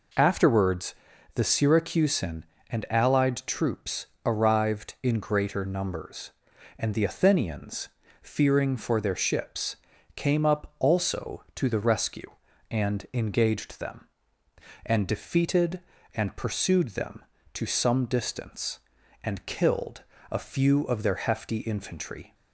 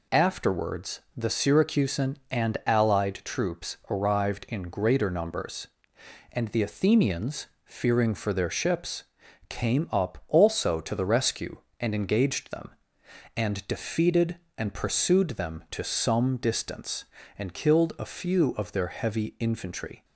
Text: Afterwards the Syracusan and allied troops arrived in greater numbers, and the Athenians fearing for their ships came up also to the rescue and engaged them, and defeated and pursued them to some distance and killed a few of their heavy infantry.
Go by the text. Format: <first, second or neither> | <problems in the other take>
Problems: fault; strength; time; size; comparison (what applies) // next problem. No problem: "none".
second | pauses between "Afterwards" and "the"; at 0.9 s; 0.40 s long; slight in the second // pauses between "troops" and "arrived"; slight; at 4.0 s; 0.18 s long // pauses between "Athenians" and "fearing"; slight; at 7.8 s; 0.32 s long; slight in the second // pauses between "ships" and "came"; at 9.7 s; 0.38 s long; also in the second // pauses between "killed" and "a"; slight; at 20.0 s; 0.28 s long // says "hefty" for "heavy"; at 21.1 s